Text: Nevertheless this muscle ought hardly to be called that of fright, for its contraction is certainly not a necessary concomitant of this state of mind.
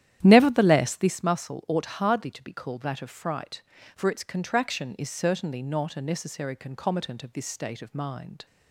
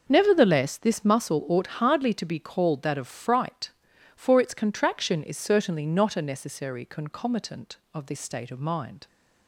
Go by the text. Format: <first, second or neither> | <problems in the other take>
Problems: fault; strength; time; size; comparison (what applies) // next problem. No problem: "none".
second | starts louder than the rest; strong; until 1.2 s; 11 dB